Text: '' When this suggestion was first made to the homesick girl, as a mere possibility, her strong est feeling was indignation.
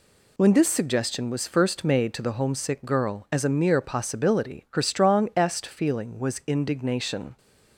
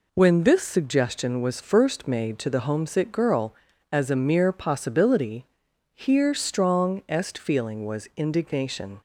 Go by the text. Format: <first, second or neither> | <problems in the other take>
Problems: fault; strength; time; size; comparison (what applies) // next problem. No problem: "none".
first | says "here" for "her"; at 5.9 s